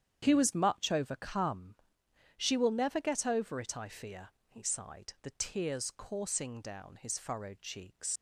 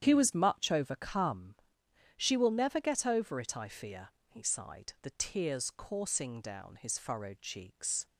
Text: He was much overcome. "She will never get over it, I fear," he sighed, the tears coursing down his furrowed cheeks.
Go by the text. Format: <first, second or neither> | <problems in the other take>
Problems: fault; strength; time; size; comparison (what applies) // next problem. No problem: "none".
second | starts louder than the rest; strong; until 1.2 s; 9 dB; strong in the second // leaves "cheeks" unfinished; at 8.1 s; 95 ms